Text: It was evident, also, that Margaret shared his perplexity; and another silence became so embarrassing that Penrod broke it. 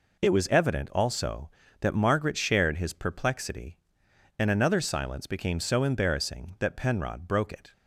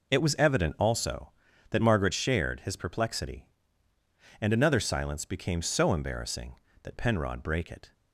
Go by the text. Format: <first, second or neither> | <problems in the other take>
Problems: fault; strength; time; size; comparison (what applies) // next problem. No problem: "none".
first | says "brake" for "broke"; at 7.4 s